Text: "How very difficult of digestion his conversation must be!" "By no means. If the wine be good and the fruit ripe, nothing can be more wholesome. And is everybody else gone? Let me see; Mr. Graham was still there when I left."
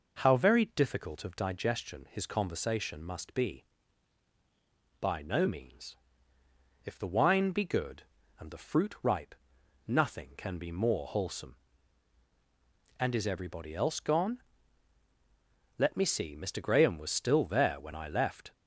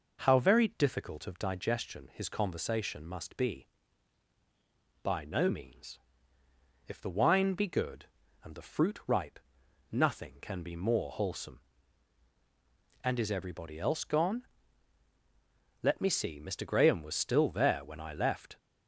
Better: neither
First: none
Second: none

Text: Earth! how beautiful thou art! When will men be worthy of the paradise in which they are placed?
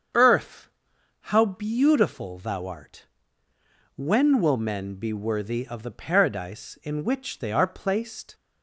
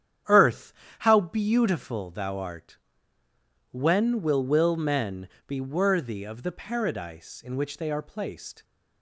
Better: first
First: starts louder than the rest; strong; until 1.6 s; 7.5 dB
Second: starts louder than the rest; strong; until 1.5 s; 9.5 dB // says "will" twice; at 4.4 s // pauses between "men" and "be"; slight; at 5.2 s; 0.20 s long

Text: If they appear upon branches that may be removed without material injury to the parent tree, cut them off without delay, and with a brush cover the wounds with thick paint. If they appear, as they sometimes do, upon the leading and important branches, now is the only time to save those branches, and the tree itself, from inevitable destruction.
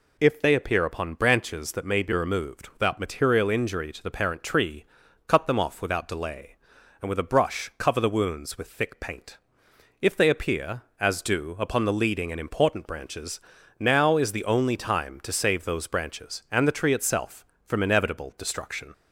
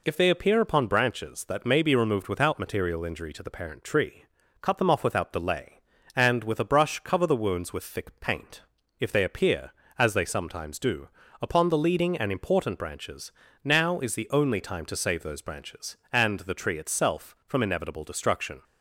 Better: second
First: skips "they sometimes"; at 11.2 s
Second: none

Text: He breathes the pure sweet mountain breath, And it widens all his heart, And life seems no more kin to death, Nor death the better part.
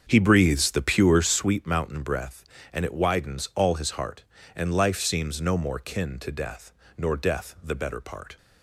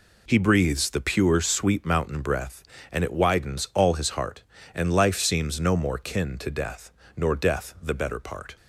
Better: second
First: starts louder than the rest; until 1.6 s; 7 dB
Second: none

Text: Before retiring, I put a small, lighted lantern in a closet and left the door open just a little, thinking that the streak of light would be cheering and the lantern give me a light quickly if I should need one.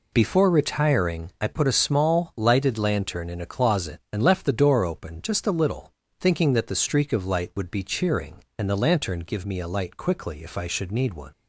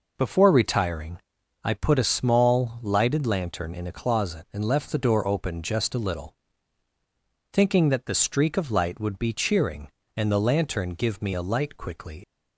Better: first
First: none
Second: stops before "if I should need one"; at 12.2 s

